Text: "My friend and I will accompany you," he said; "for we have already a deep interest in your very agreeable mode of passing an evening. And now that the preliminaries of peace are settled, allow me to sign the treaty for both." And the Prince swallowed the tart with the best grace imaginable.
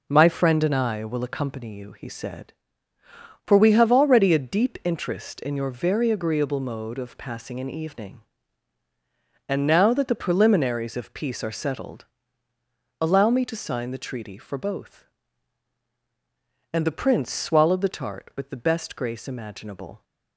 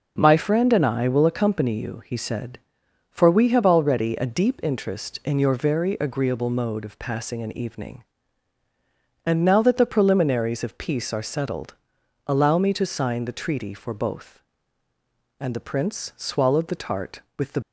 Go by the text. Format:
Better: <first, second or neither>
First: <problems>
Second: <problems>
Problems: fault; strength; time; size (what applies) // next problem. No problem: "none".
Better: first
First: none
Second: stops before "best grace imaginable"; at 17.6 s